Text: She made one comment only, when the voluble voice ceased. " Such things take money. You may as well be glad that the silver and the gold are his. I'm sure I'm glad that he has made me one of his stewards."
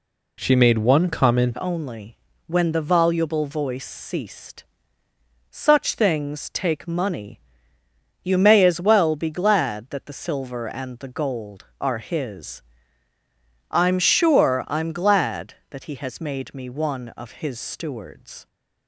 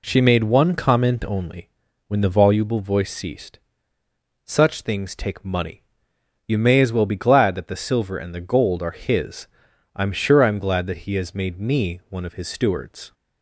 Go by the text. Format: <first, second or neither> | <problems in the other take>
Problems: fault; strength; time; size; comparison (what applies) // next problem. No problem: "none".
second | changes voice at "only"; from 1.5 s on; 16.9 s long